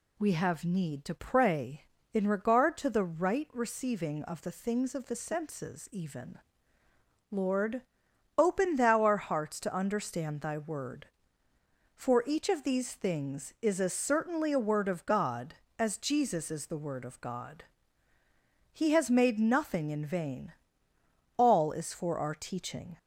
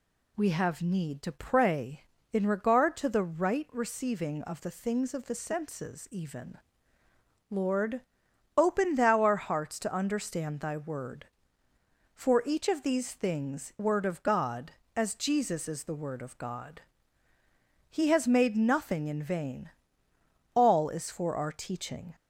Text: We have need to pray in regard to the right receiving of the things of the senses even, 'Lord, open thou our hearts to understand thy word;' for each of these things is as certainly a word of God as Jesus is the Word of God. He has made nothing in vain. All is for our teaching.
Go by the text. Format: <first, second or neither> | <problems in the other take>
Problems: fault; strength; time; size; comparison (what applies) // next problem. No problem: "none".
first | skips "is as certainly a"; at 13.7 s